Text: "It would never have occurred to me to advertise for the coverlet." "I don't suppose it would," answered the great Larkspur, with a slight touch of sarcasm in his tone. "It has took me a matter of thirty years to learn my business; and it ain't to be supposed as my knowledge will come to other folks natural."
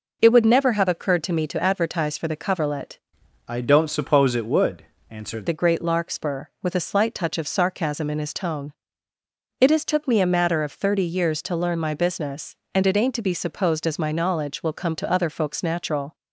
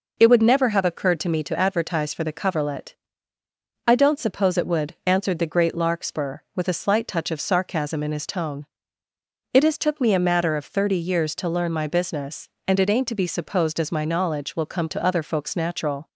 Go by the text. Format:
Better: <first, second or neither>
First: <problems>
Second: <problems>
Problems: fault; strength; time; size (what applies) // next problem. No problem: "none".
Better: second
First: changes voice from "I" to "answered"; from 3.4 to 5.4 s; 2.0 s long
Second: none